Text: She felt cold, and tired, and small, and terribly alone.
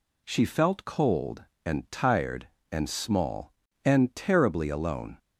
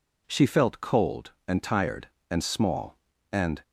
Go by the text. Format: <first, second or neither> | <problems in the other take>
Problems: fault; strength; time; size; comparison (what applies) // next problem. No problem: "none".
first | stops before "terribly alone"; at 3.6 s